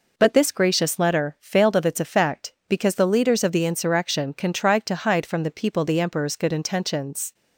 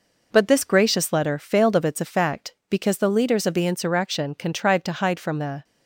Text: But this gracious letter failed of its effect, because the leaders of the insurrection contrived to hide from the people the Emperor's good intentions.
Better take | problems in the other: first | stops before "people the Emperor's good intentions"; at 5.6 s

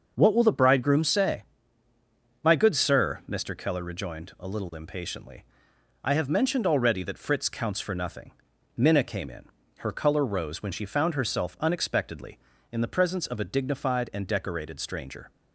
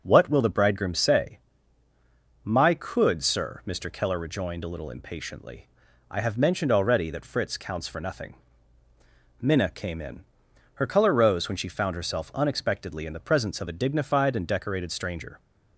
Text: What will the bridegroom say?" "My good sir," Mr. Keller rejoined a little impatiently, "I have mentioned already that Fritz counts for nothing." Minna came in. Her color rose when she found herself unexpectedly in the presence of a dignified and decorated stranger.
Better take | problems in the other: first | starts louder than the rest; until 1.0 s; 6 dB; also in the first // says "could" for "good"; at 2.7 s

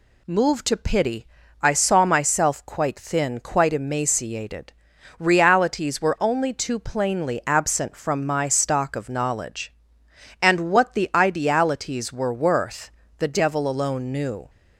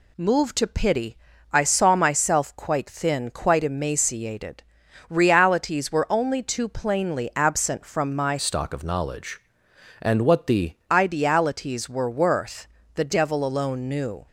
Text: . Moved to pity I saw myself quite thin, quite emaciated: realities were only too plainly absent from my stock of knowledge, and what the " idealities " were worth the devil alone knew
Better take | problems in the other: first | pauses between "pity" and "I"; slight; at 1.1 s; 0.34 s long; slight in the first // changes voice from "stock" to "the"; from 8.3 to 10.7 s; 2.4 s long // pauses between "worth" and "the"; slight; at 12.6 s; 0.30 s long; slight in the first

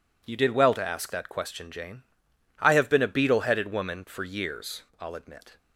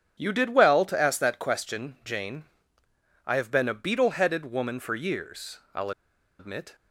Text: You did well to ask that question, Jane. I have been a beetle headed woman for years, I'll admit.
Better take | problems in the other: first | pauses between "I'll" and "admit"; noticeable; at 5.9 s; 0.47 s long

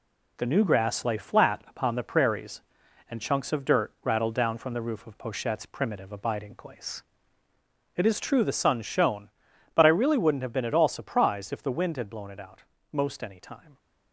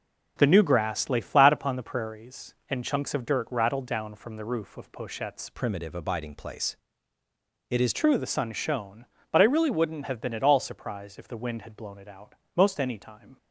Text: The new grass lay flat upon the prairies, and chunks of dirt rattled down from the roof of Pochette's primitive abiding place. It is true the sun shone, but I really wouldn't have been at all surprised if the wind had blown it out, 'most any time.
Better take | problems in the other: first | changes voice from "primitive" to "is"; from 5.5 to 7.9 s; 2.4 s long

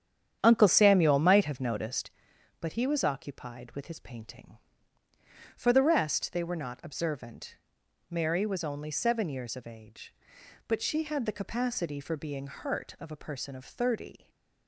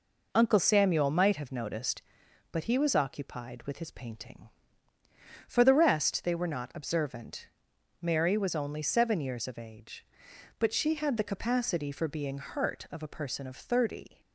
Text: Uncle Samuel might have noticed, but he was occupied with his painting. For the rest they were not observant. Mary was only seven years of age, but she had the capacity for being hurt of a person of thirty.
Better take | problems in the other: second | starts louder than the rest; strong; until 2.0 s; 9 dB // stays silent after the last word; slight; from 14.1 s on; 0.5 s long

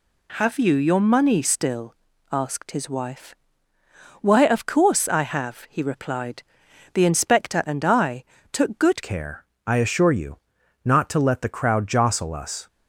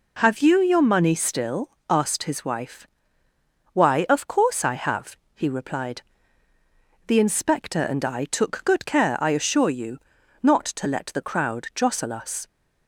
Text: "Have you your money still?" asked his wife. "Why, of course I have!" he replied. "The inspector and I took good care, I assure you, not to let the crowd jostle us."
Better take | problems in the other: second | pauses between "I" and "took"; slight; at 8.2 s; 0.30 s long // changes voice at "care"; from 9.0 s on; 3.6 s long

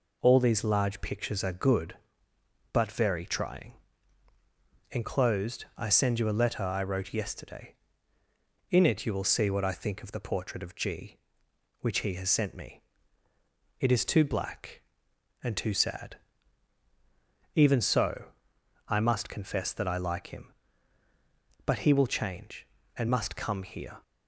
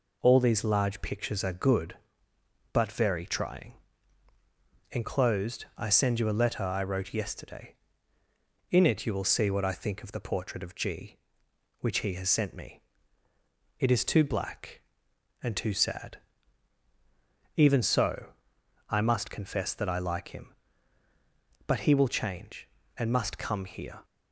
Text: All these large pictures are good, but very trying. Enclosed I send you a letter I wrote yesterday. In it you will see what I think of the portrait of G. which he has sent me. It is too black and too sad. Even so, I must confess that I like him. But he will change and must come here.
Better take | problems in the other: neither | none

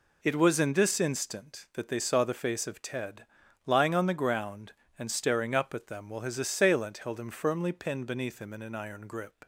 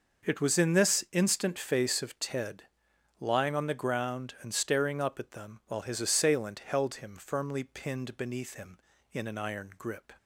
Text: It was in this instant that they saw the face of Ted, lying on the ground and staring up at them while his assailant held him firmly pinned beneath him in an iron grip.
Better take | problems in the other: first | skips "that they saw the"; at 1.5 s

